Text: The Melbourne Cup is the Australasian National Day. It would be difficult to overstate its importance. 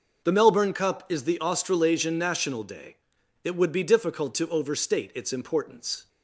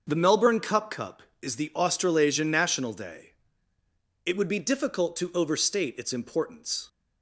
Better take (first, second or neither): first